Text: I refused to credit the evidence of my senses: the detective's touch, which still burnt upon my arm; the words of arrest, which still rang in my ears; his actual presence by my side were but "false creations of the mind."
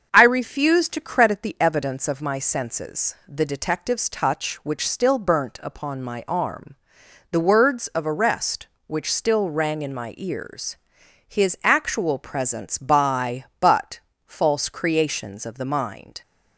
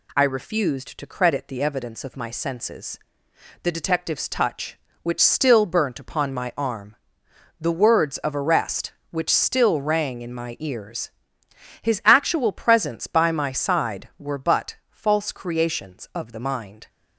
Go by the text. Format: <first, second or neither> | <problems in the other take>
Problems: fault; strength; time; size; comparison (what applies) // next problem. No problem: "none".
second | starts louder than the rest; until 1.1 s; 7 dB // skips "my side were"; at 13.5 s // pauses between "but" and "false"; slight; at 13.9 s; 0.26 s long